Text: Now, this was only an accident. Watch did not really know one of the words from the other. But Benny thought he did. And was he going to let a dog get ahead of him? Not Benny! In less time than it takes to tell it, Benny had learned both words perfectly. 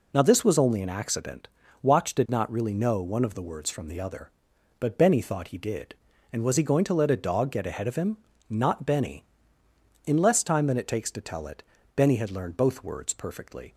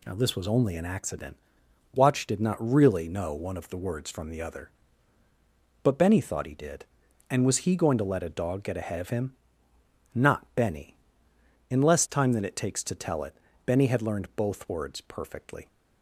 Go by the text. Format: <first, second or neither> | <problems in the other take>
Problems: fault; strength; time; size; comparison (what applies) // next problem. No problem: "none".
neither | none